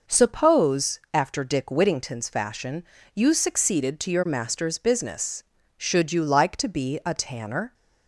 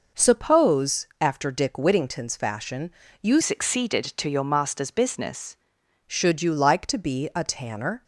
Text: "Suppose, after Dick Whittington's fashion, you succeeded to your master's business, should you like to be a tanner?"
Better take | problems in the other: first | changes voice from "succeeded" to "business"; from 3.4 to 5.5 s; 2.1 s long

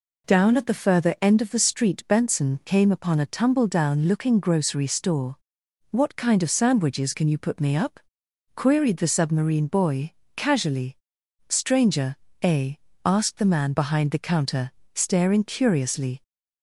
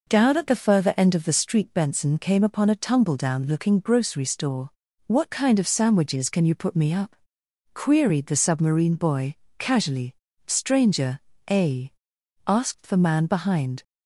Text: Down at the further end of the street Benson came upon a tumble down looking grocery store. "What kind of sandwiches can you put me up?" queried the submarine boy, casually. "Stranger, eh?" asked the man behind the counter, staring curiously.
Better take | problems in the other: first | stops before "the counter staring curiously"; at 13.8 s

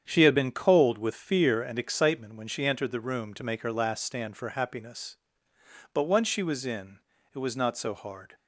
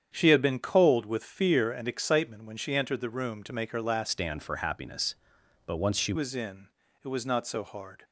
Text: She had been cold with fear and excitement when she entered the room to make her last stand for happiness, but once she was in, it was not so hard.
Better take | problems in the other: first | starts louder than the rest; strong; until 1.1 s; 8.5 dB; strong in the first // changes voice from "stand" to "she"; from 4.0 to 6.1 s; 2.1 s long

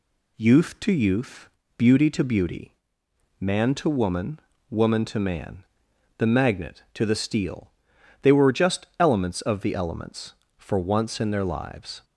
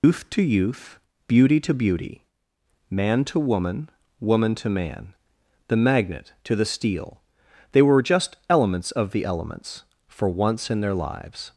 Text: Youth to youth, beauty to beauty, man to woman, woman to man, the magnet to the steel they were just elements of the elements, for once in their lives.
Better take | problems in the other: first | loses the start of "Youth"; at 0.0 s; 180 ms // pauses between "steel" and "they"; noticeable; at 7.1 s; 0.52 s long; noticeable in the first

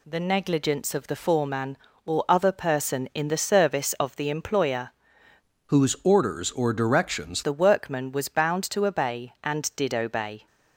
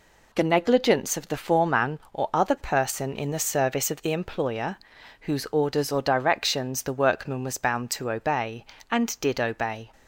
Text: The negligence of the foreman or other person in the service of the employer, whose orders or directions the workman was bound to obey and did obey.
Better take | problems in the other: second | changes voice from "whose" to "directions"; from 5.6 to 7.4 s; 1.8 s long

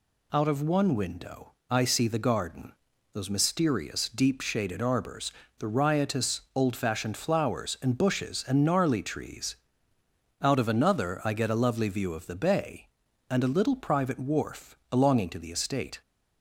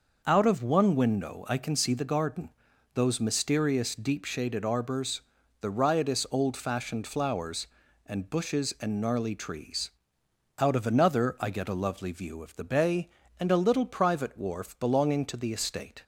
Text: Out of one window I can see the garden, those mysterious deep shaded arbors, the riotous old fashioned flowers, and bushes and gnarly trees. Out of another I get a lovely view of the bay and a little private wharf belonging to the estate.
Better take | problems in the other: second | pauses between "window" and "I"; slight; at 1.5 s; 0.18 s long // skips "can"; at 1.8 s

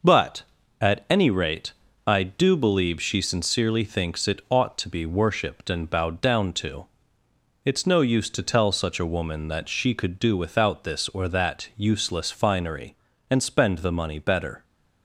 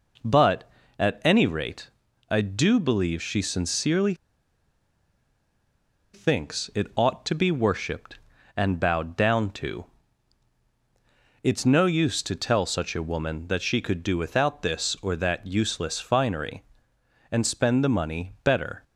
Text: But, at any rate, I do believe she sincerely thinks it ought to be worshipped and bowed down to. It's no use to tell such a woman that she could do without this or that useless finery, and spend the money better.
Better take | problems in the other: first | pauses between "sincerely" and "thinks"; strong; at 4.1 s; 1.9 s long

